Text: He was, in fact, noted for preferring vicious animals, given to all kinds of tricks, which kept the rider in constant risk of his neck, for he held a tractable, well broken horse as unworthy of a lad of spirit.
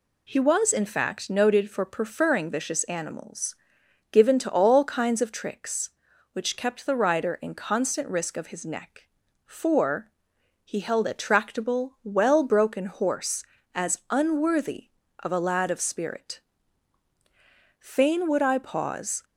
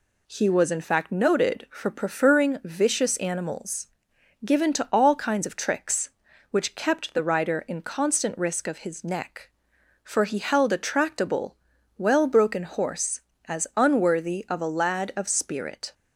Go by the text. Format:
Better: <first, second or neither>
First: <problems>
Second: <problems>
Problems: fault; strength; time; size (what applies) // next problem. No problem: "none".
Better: second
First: pauses between "for" and "he"; noticeable; at 10.1 s; 0.54 s long // goes on to say "Fain would I pause"; from 17.7 s on; 1.4 s long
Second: none